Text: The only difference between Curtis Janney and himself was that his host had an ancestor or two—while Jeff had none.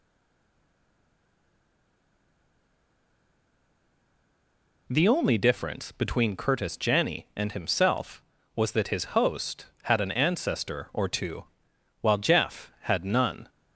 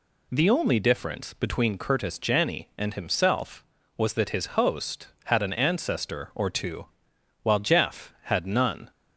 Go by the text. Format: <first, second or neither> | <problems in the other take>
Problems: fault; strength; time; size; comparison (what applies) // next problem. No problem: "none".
second | stays silent before the first word; strong; until 4.8 s; 4.8 s long